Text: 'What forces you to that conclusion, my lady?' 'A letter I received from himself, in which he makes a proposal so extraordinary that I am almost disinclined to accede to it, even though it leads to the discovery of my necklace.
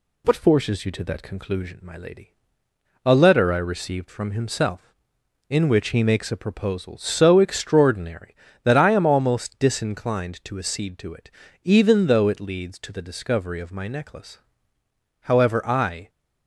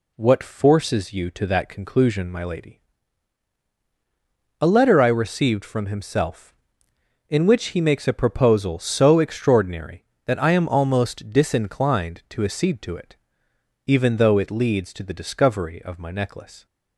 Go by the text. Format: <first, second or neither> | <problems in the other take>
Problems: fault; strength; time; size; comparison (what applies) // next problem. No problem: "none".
second | goes on to say "However I"; noticeable; from 15.2 s on; 0.88 s long